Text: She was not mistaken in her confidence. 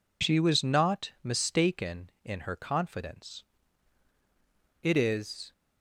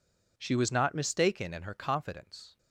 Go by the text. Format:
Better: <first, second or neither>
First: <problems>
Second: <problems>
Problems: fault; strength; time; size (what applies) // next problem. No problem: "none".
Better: second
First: goes on to say "It is"; noticeable; from 4.8 s on; 0.68 s long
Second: none